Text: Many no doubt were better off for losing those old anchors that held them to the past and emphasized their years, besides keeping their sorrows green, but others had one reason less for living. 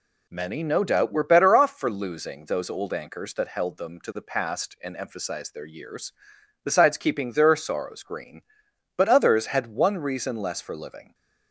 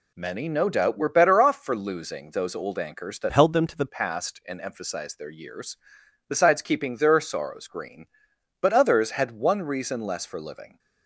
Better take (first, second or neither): first